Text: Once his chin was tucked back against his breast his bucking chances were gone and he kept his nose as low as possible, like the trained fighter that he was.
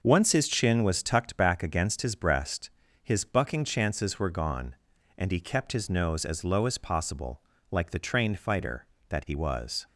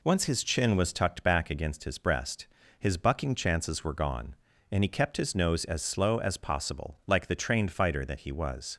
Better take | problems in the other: first | pauses between "breast" and "his"; slight; at 2.4 s; 0.32 s long; slight in the first // says "slow" for "low"; at 5.8 s

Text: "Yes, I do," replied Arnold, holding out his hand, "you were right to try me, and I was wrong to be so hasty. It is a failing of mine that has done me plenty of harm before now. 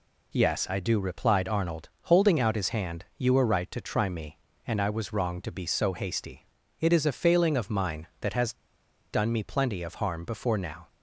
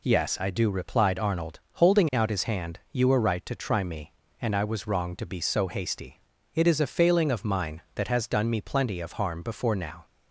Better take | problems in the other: second | pauses between "has" and "done"; noticeable; at 8.5 s; 0.57 s long

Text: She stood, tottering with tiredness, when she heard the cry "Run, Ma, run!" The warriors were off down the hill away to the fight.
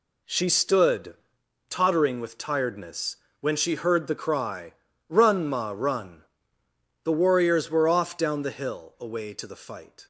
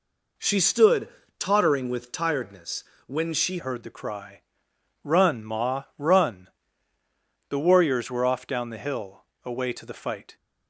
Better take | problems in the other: first | changes voice at "heard"; from 3.5 s on; 6.8 s long // pauses between "cry" and "Run"; noticeable; at 4.4 s; 0.60 s long; also in the first // pauses between "hill" and "away"; slight; at 9.2 s; 0.22 s long

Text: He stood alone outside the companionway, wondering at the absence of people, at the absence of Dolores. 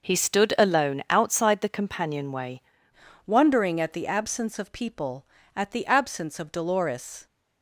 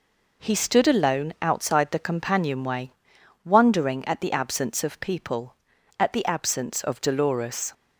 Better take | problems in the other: second | starts louder than the rest; noticeable; until 1.1 s; 6 dB // changes voice at "wondering"; from 3.2 s on; 4.0 s long

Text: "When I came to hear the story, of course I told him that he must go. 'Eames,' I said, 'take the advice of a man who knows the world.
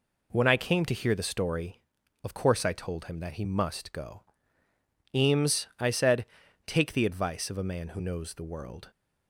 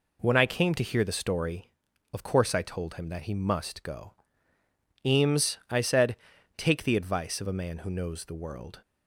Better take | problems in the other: neither | none

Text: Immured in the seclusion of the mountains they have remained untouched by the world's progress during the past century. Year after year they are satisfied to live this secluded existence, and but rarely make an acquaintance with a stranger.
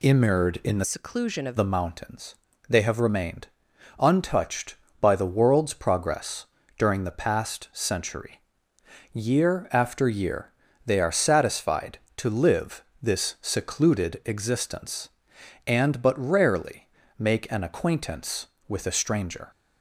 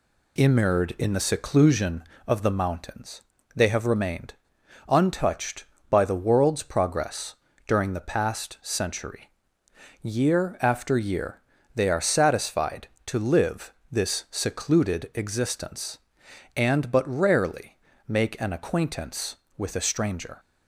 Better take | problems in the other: second | changes voice from "seclusion" to "of"; from 0.8 to 1.5 s; 0.7 s long // pauses between "mountains" and "they"; slight; at 2.3 s; 0.32 s long; slight in the second // pauses between "remained" and "untouched"; noticeable; at 3.4 s; 0.50 s long; noticeable in the second // pauses between "progress" and "during"; slight; at 6.4 s; 0.32 s long; slight in the second // pauses between "year" and "they"; slight; at 10.5 s; 0.34 s long; slight in the second // pauses between "live" and "this"; slight; at 12.8 s; 0.18 s long; slight in the second // pauses between "rarely" and "make"; slight; at 16.8 s; 0.32 s long; slight in the second

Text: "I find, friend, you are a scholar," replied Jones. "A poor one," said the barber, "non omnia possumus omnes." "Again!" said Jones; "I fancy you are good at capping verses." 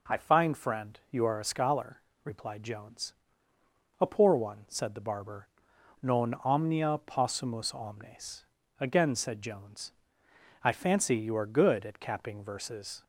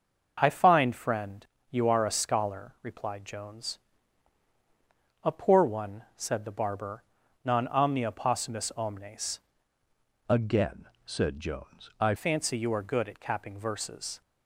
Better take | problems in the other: first | starts louder than the rest; until 1.4 s; 6 dB // changes voice from "Again" to "I"; from 10.2 to 12.1 s; 1.9 s long

